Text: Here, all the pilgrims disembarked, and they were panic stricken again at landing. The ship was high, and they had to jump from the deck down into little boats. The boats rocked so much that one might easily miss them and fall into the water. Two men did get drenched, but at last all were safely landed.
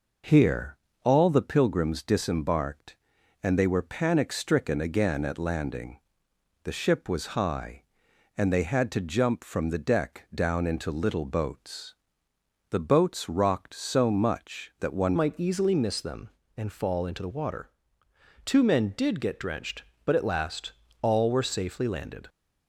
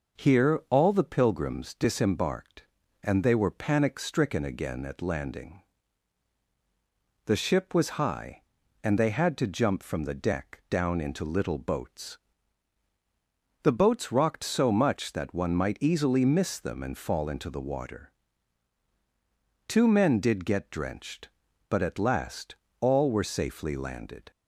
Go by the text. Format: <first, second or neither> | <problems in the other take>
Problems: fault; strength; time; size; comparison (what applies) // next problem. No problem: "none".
second | changes voice at "might"; from 15.1 s on; 7.1 s long // pauses between "last" and "all"; slight; at 20.7 s; 0.30 s long; slight in the second